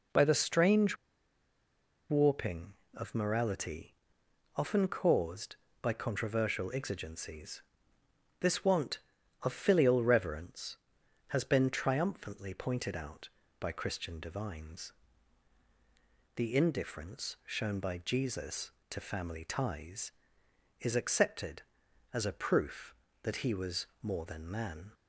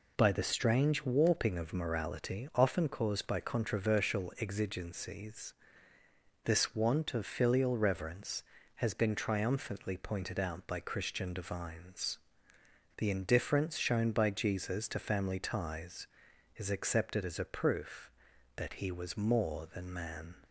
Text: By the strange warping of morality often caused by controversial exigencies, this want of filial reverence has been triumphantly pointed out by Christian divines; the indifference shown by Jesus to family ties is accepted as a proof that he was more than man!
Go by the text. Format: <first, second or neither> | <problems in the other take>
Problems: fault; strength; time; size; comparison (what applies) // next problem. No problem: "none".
second | pauses between "strange" and "warping"; at 0.9 s; 1.1 s long // pauses between "morality" and "often"; noticeable; at 3.9 s; 0.62 s long // pauses between "was" and "more"; slight; at 23.8 s; 0.16 s long